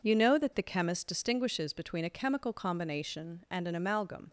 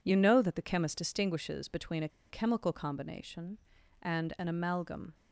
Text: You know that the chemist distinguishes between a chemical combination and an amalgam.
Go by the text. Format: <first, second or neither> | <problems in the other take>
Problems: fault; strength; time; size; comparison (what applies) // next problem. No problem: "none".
first | pauses between "a" and "chemical"; slight; at 2.0 s; 0.20 s long